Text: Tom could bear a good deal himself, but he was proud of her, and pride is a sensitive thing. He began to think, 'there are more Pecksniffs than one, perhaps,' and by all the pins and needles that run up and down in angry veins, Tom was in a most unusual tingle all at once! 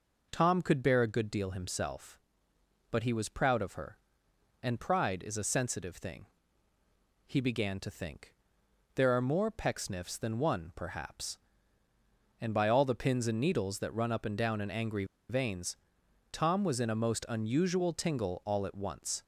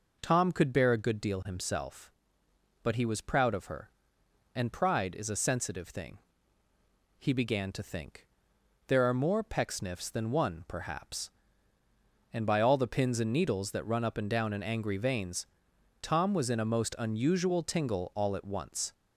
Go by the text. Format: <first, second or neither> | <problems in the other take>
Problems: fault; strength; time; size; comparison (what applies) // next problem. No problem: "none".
second | pauses between "angry" and "veins"; slight; at 15.0 s; 0.25 s long